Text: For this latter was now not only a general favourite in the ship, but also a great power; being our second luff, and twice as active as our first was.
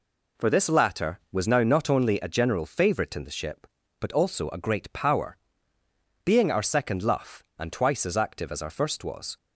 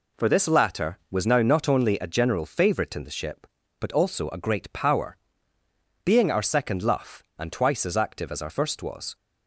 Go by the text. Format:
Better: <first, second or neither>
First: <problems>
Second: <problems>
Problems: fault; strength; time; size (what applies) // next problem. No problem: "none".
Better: neither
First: none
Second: none